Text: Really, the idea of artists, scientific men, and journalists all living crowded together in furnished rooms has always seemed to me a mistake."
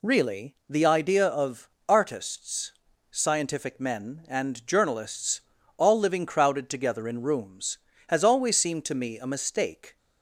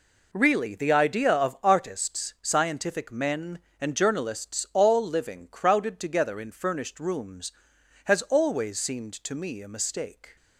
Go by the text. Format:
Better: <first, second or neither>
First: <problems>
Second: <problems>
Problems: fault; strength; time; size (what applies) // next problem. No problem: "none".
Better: second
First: pauses between "of" and "artists"; slight; at 1.6 s; 0.20 s long // pauses between "journalists" and "all"; slight; at 5.4 s; 0.34 s long // skips "furnished"; at 7.2 s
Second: none